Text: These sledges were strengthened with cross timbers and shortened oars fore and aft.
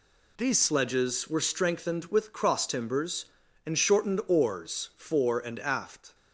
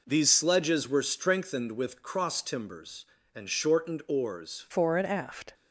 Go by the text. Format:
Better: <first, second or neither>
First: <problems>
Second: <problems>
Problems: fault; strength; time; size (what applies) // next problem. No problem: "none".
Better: first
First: none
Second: changes voice at "fore"; from 4.7 s on; 0.8 s long